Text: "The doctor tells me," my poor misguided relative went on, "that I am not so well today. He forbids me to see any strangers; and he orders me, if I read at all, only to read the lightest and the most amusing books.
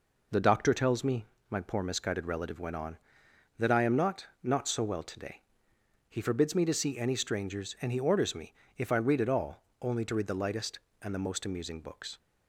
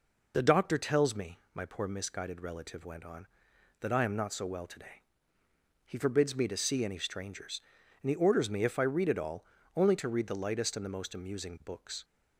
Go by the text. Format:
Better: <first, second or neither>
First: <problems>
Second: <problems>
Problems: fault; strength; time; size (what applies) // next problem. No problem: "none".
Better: second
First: says "not" twice; at 4.4 s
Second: none